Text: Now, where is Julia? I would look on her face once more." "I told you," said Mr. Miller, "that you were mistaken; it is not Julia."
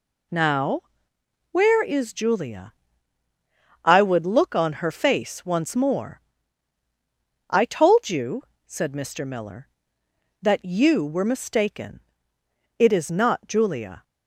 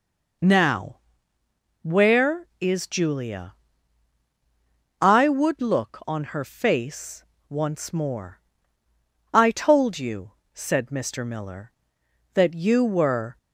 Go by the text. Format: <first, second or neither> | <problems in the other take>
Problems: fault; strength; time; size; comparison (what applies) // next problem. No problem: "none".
first | pauses between "face" and "once"; slight; at 7.2 s; 0.26 s long // stops before "mistaken it is not Julia"; at 13.3 s